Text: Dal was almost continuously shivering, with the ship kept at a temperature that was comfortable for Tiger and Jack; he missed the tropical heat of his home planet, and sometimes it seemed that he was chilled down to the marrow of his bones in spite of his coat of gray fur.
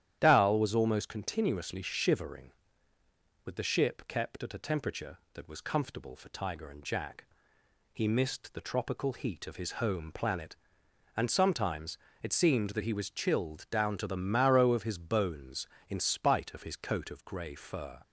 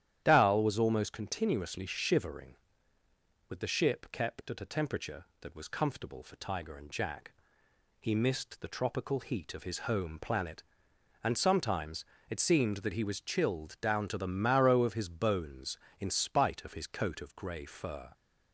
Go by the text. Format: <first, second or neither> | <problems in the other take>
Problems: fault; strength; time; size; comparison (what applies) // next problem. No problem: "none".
neither | starts louder than the rest; strong; the same in both // pauses between "sometimes" and "it"; slight; the same in both